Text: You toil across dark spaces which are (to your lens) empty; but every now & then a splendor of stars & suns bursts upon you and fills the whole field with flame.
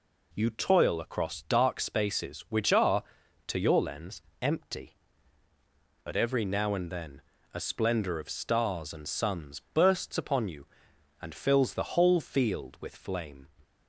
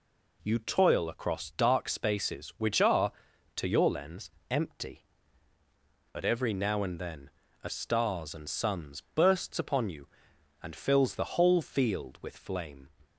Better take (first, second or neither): first